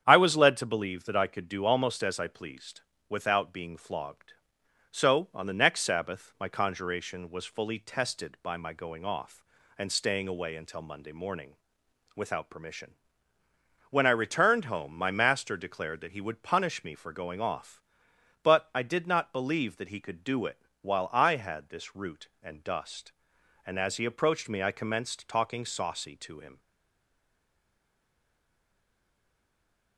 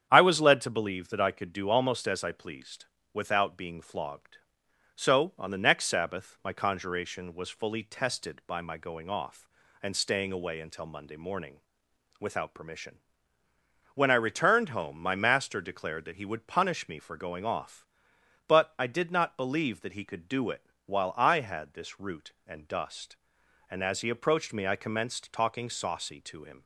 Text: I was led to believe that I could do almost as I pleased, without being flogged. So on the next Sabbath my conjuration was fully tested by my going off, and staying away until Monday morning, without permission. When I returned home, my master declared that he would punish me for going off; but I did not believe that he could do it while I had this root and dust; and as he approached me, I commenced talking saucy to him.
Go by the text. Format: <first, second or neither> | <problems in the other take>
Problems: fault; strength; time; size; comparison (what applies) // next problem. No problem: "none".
second | starts louder than the rest; strong; until 1.0 s; 8.5 dB; strong in the second // pauses between "it" and "while"; slight; at 20.5 s; 0.22 s long; slight in the second // stays silent after the last word; strong; from 26.5 s on; 3.4 s long